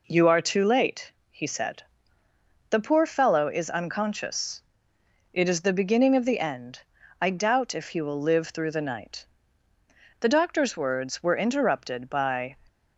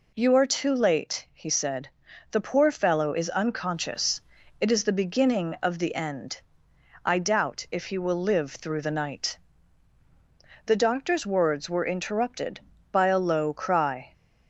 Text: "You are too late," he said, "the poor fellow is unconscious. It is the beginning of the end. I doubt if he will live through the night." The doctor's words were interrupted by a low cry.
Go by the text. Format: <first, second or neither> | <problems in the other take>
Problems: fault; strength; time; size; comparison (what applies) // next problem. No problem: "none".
second | stops before "a low cry"; at 12.6 s